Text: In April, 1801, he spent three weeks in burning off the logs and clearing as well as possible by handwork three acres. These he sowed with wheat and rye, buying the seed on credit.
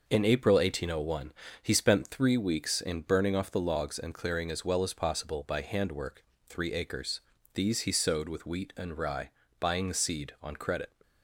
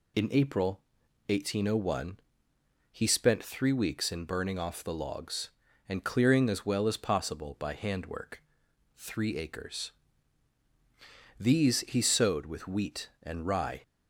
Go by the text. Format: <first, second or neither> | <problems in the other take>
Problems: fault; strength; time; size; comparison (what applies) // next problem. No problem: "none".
first | pauses between "handwork" and "three"; noticeable; at 8.4 s; 0.54 s long; slight in the first // stops before "buying the seed on credit"; at 13.8 s